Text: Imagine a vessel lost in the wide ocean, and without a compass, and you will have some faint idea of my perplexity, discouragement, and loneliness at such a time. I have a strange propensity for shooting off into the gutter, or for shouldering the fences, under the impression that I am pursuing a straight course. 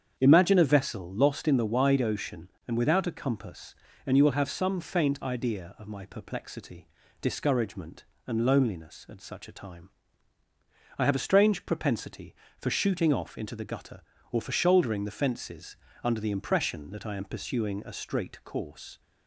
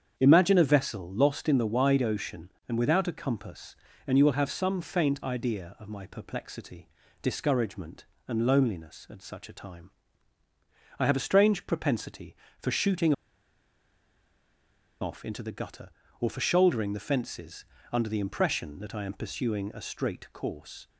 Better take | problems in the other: first | starts louder than the rest; strong; until 1.1 s; 7.5 dB; strong in the first // pauses between "shooting" and "off"; strong; at 13.1 s; 1.8 s long

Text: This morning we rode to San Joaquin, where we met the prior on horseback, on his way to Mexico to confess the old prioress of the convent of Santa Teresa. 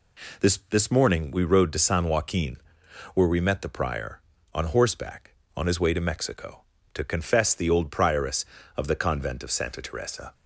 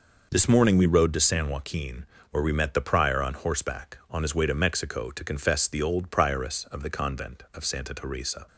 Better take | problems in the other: second | says "This" twice; at 0.6 s

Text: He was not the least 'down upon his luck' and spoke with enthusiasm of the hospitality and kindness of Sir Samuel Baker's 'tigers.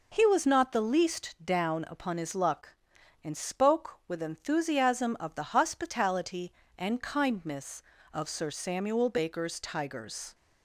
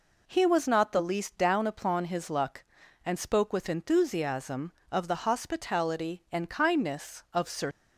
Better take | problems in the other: first | stops before "Samuel Baker's tigers"; at 7.7 s

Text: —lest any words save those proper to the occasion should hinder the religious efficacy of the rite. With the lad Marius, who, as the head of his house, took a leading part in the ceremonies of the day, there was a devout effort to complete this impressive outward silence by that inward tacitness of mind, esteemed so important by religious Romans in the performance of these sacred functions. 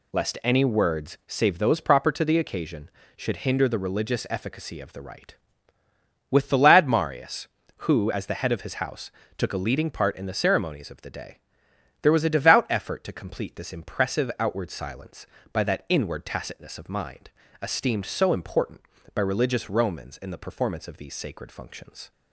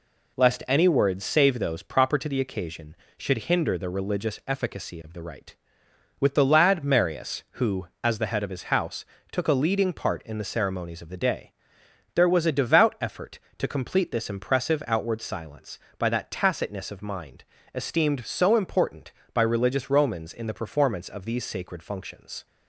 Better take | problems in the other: first | skips "inward"; at 16.3 s

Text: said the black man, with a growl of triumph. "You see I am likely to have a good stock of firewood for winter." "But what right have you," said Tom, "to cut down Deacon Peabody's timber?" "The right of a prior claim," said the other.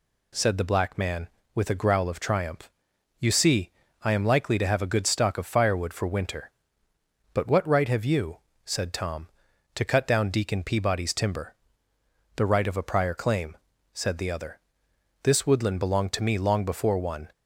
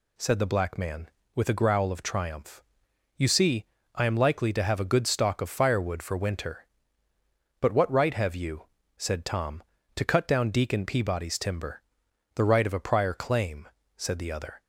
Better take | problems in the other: second | pauses between "see" and "I"; slight; at 3.6 s; 0.32 s long; slight in the second // goes on to say "This woodland belonged to me long before one"; strong; from 15.2 s on; 2.0 s long

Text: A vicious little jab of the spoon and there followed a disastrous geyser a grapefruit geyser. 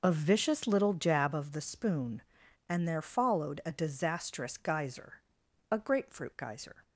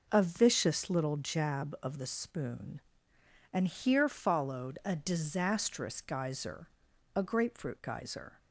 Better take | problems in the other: first | says "here" for "there"; at 3.6 s // pauses between "geyser" and "a"; noticeable; at 6.6 s; 0.46 s long; noticeable in the first

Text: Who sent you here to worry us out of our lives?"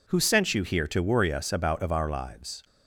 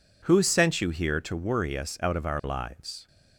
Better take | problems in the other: second | says "about" for "out"; at 1.5 s

